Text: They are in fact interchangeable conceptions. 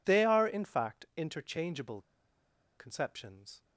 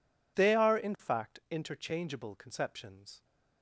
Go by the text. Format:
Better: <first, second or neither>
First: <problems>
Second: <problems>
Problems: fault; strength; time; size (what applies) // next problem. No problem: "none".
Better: second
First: pauses between "interchangeable" and "conceptions"; noticeable; at 1.9 s; 0.76 s long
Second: none